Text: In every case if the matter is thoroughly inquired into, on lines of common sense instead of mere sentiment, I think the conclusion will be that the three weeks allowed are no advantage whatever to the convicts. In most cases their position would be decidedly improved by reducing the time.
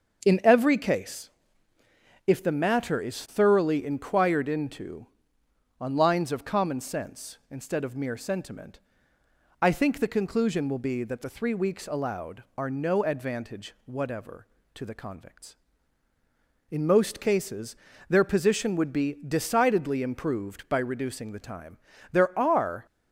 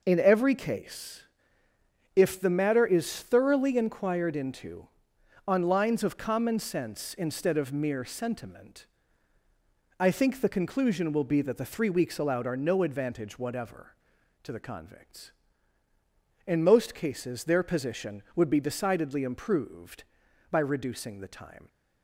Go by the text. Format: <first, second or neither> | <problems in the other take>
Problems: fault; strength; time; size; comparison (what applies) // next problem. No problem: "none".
second | starts louder than the rest; until 1.3 s; 6.5 dB // pauses between "case" and "if"; noticeable; at 1.2 s; 0.96 s long; noticeable in the second // pauses between "cases" and "their"; slight; at 17.7 s; 0.32 s long // goes on to say "There are"; noticeable; from 22.1 s on; 0.74 s long